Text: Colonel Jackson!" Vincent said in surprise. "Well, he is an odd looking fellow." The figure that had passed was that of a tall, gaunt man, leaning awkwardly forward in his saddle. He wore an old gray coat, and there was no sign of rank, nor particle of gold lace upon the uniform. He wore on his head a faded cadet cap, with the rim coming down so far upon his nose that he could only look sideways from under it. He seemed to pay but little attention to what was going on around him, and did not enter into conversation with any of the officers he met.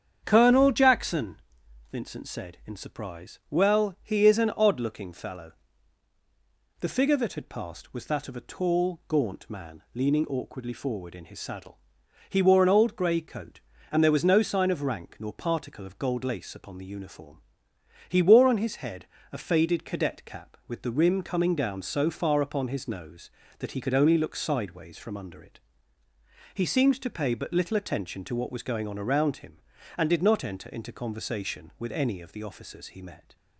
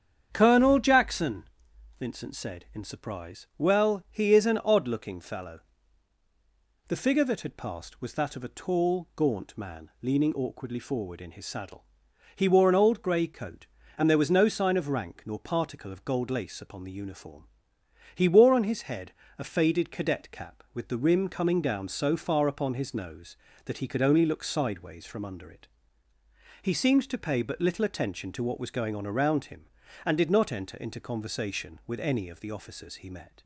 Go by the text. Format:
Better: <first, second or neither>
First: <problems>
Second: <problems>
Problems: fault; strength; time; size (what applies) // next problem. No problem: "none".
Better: neither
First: starts louder than the rest; strong; until 1.2 s; 8 dB // pauses between "head" and "a"; slight; at 19.0 s; 0.26 s long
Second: starts louder than the rest; strong; until 1.3 s; 8 dB // pauses between "head" and "a"; slight; at 19.1 s; 0.26 s long